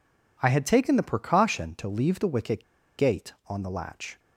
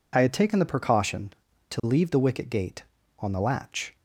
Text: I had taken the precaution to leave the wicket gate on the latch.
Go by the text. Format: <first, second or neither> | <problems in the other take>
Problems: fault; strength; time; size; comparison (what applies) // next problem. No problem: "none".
second | pauses between "wicket" and "gate"; slight; at 2.6 s; 0.34 s long